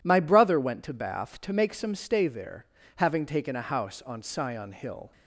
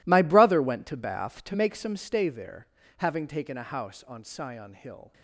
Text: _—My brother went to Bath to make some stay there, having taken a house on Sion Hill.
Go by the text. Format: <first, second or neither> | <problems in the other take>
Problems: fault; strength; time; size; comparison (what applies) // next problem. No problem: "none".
first | gets quieter; strong; throughout; 16 dB